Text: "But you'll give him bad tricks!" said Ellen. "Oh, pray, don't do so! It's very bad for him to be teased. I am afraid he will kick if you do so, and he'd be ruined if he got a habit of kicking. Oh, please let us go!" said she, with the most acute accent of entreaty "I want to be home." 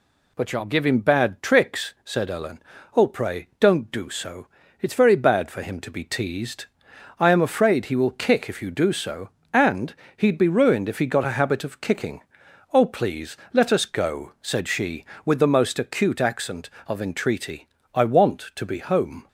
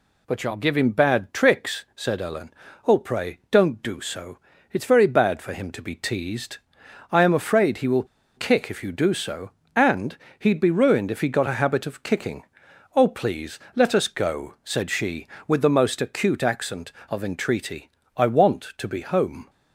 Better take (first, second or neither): first